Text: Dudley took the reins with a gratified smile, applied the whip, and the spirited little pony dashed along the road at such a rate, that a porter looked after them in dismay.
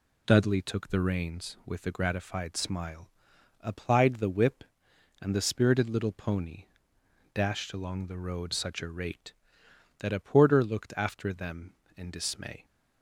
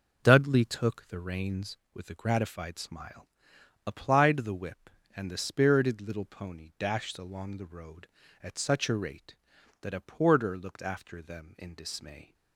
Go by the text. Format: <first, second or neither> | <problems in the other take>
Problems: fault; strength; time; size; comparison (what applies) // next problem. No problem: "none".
second | pauses between "pony" and "dashed"; noticeable; at 6.6 s; 0.70 s long // skips "at"; at 8.5 s